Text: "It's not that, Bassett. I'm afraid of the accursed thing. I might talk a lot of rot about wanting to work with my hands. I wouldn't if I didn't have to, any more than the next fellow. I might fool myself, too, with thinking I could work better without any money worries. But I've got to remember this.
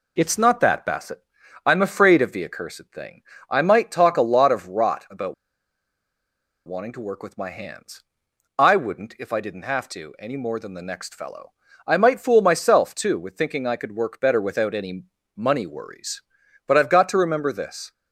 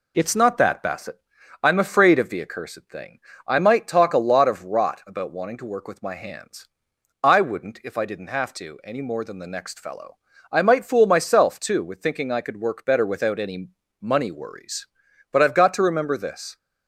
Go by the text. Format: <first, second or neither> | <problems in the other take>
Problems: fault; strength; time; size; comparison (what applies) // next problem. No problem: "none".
second | pauses between "about" and "wanting"; strong; at 5.3 s; 1.3 s long // pauses between "any" and "money"; slight; at 15.0 s; 0.30 s long; slight in the second